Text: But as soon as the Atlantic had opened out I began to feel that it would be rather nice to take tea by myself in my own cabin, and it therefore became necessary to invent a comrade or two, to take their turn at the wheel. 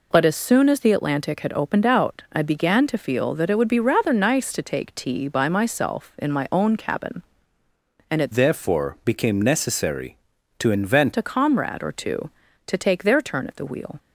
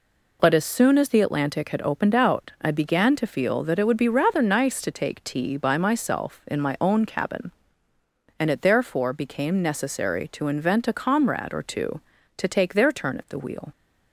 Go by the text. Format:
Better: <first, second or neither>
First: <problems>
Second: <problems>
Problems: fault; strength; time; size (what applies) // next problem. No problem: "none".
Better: second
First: changes voice from "therefore" to "invent"; from 8.3 to 11.1 s; 2.8 s long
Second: none